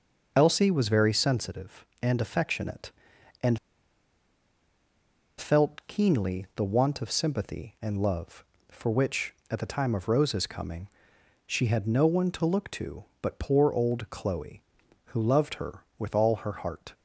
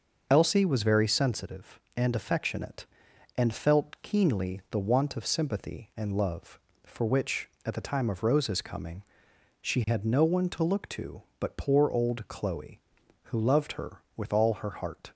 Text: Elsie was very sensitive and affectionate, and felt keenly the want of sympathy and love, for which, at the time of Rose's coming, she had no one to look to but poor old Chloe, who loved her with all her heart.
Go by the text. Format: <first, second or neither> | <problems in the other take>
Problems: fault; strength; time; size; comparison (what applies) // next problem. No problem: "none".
second | pauses between "and" and "felt"; strong; at 3.5 s; 1.7 s long